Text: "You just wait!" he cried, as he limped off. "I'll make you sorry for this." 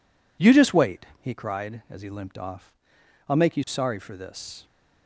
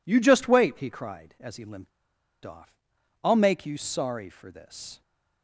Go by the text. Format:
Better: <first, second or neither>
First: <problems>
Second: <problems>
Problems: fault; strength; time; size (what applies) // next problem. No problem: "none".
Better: first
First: none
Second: pauses between "limped" and "off"; noticeable; at 1.9 s; 0.55 s long